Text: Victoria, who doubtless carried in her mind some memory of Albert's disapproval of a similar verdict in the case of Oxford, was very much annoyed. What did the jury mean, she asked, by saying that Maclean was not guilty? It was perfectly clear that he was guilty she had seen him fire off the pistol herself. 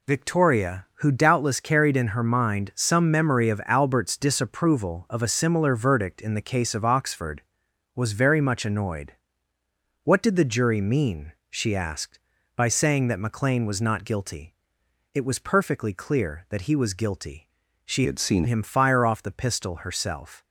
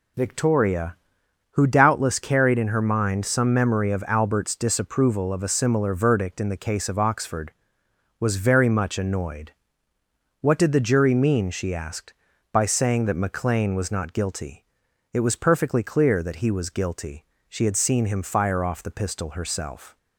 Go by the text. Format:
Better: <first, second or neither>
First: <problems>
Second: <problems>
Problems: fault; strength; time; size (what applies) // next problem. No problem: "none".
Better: second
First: pauses between "guilty" and "she"; at 17.4 s; 0.38 s long // changes voice from "had" to "seen"; from 18.0 to 18.4 s; 0.4 s long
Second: pauses between "guilty" and "she"; slight; at 17.2 s; 0.24 s long